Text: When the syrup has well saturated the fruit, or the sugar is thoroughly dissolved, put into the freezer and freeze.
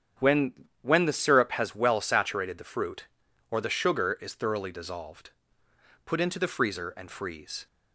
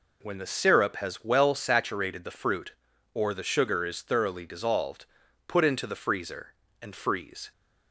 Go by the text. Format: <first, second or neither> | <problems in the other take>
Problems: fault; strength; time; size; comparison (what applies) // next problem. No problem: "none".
second | starts louder than the rest; strong; until 1.4 s; 9 dB // says "When" twice; at 0.8 s